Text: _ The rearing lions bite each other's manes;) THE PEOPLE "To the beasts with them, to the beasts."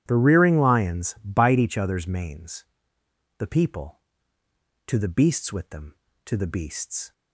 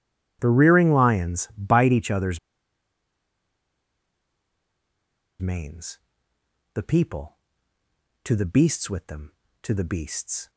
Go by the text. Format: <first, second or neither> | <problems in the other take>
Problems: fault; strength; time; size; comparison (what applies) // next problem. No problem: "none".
first | starts louder than the rest; strong; until 1.4 s; 11.5 dB; strong in the first // pauses between "other's" and "manes"; strong; at 2.3 s; 3.0 s long